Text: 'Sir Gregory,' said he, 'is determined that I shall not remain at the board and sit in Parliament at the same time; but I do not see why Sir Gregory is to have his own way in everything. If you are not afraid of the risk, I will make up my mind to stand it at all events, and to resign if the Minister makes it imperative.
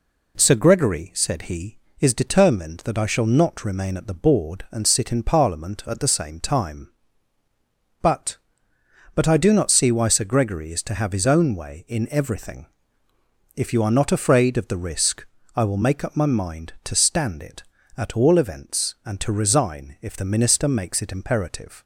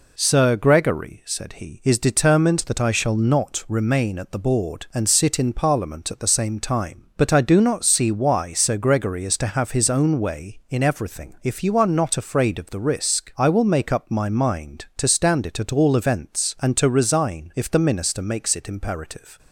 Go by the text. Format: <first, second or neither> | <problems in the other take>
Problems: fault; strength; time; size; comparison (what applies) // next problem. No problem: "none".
second | says "but" twice; at 9.1 s